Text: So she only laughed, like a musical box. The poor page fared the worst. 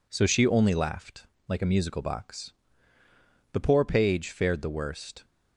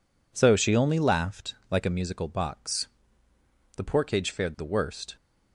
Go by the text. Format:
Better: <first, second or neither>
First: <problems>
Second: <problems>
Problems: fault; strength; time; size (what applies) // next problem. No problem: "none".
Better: first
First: none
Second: says "cage" for "page"; at 4.0 s